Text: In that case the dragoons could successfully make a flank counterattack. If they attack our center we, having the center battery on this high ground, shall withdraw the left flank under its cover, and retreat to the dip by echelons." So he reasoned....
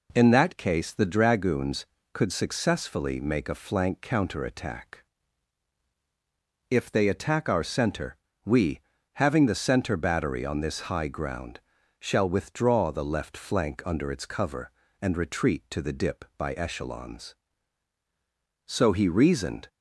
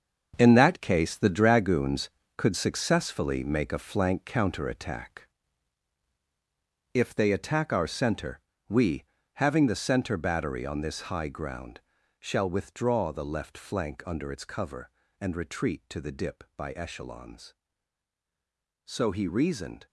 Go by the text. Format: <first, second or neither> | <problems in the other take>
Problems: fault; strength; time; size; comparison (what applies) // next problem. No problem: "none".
first | gets quieter; strong; throughout; 10 dB // pauses between "center" and "we"; slight; at 8.4 s; 0.28 s long; slight in the first